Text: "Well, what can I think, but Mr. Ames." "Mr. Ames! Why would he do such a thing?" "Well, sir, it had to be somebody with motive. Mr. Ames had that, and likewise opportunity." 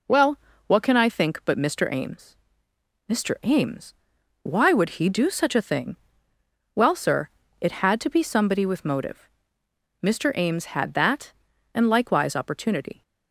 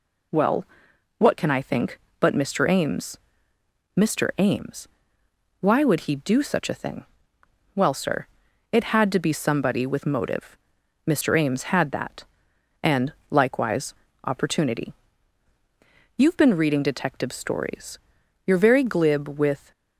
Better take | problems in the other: first | pauses between "and" and "likewise"; slight; at 13.1 s; 0.16 s long // pauses between "likewise" and "opportunity"; slight; at 13.9 s; 0.32 s long // goes on to say "You've been reading detective stories You're very glib with"; strong; from 16.1 s on; 3.5 s long

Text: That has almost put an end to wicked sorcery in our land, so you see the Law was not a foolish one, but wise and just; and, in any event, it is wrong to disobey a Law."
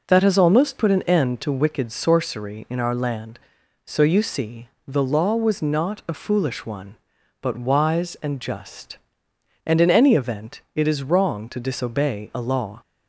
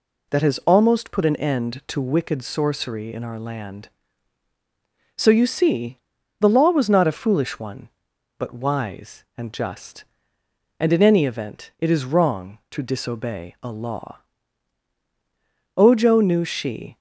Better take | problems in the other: first | pauses between "see" and "the"; at 5.9 s; 0.44 s long; slight in the first // goes on to say "Ojo knew she"; noticeable; from 15.7 s on; 1.2 s long

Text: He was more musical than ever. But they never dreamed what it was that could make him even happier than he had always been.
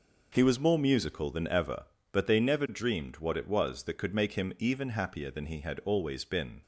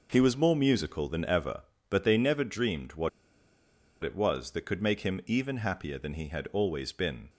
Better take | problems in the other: first | pauses between "what" and "it"; noticeable; at 3.0 s; 0.94 s long

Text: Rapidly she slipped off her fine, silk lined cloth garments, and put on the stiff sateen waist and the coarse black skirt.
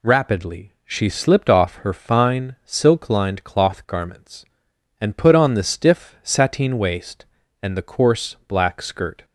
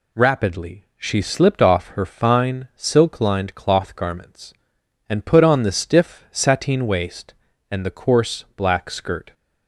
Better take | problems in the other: neither | none

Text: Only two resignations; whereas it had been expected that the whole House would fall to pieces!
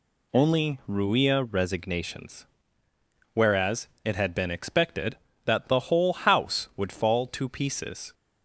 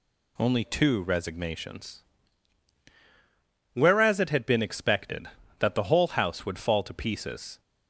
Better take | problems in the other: second | says "ruia" for "two"; at 0.8 s // pauses between "whereas" and "it"; slight; at 3.8 s; 0.16 s long

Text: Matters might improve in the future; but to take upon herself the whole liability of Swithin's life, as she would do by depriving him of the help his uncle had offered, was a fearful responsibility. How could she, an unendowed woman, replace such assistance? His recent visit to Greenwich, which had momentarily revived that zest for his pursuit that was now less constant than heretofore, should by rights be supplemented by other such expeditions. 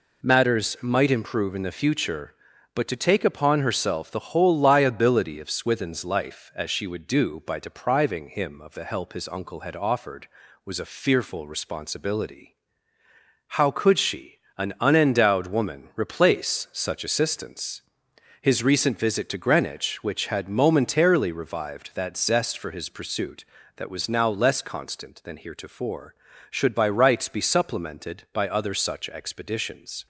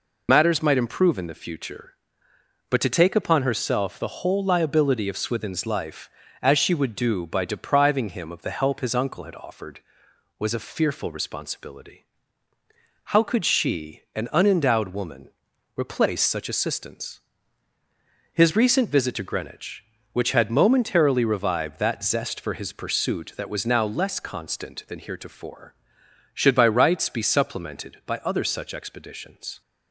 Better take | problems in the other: first | loses the start of "Matters"; at 0.2 s; 60 ms

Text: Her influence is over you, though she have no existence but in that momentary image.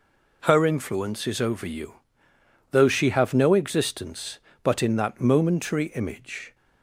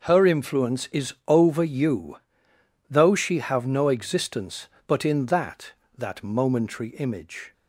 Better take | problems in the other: first | pauses between "is" and "over"; slight; at 1.1 s; 0.16 s long // says "that" twice; at 5.9 s

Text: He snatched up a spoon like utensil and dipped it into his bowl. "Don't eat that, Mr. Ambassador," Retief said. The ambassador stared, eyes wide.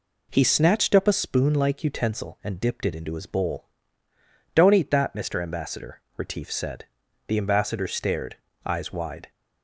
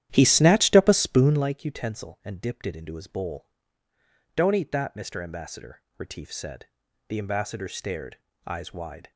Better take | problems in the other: first | starts louder than the rest; strong; until 1.5 s; 11.5 dB

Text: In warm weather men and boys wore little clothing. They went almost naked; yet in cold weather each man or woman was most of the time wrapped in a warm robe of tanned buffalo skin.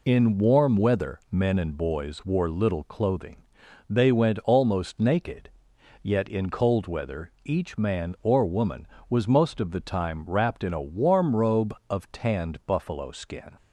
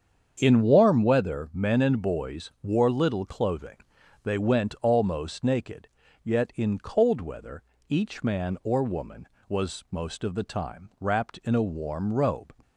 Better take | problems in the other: first | starts louder than the rest; strong; until 1.4 s; 7.5 dB // pauses between "weather" and "each"; slight; at 7.6 s; 0.24 s long // stops before "of tanned buffalo skin"; at 12.6 s

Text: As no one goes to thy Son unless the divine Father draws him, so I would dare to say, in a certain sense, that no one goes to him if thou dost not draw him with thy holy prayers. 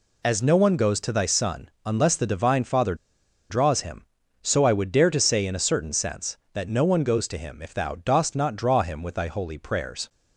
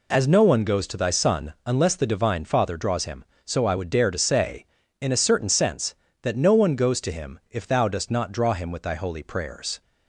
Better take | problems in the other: second | pauses between "Son" and "unless"; slight; at 1.6 s; 0.16 s long // pauses between "Father" and "draws"; noticeable; at 2.9 s; 0.55 s long

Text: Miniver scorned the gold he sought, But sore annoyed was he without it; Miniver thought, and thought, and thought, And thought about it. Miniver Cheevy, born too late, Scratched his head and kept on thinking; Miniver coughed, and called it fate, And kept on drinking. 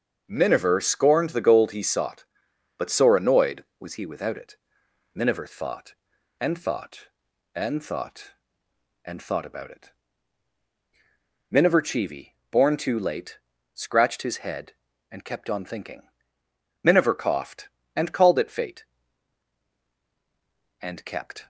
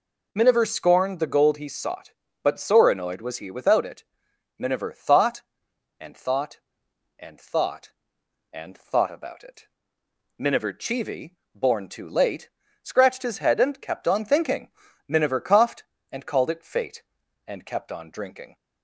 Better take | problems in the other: second | stops before "on drinking"; at 21.4 s

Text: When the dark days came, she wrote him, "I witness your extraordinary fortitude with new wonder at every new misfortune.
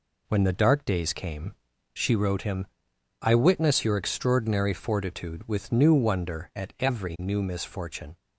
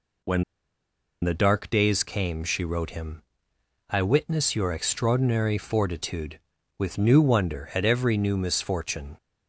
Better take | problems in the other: first | pauses between "When" and "the"; noticeable; at 0.4 s; 0.79 s long

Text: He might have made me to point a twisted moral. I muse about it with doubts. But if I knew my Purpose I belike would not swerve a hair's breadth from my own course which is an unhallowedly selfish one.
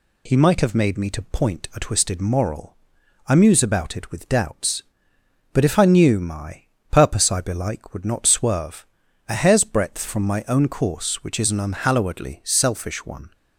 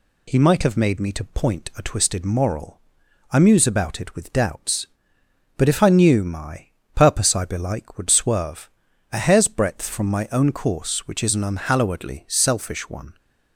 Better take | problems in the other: first | pauses between "my" and "Purpose"; slight; at 6.6 s; 0.28 s long; slight in the first // skips "not"; at 8.0 s // pauses between "swerve" and "a"; at 8.7 s; 0.42 s long; also in the first

